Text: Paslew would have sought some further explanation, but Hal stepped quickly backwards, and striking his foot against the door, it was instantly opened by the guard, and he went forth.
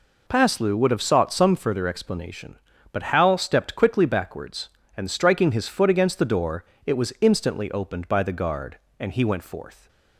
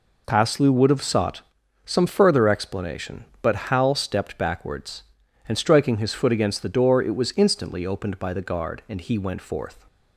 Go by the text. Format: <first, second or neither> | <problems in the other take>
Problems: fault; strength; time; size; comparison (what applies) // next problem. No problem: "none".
first | pauses between "sought" and "some"; at 1.4 s; 0.42 s long // skips "quickly"; at 4.3 s